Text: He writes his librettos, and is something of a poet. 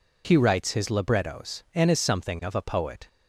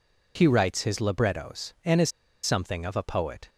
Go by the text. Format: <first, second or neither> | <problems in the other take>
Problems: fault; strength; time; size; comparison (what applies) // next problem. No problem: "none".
first | pauses between "is" and "something"; slight; at 2.1 s; 0.33 s long